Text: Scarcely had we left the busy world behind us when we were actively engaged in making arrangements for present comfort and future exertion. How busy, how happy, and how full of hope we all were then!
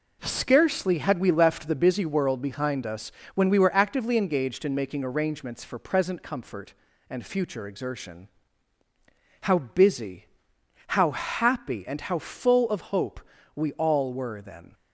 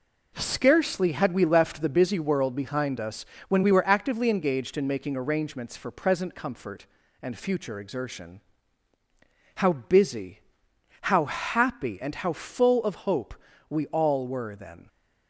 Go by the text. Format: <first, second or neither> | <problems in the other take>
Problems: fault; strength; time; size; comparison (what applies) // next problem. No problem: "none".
neither | pauses between "us" and "when"; slight; the same in both // pauses between "hope" and "we"; slight; the same in both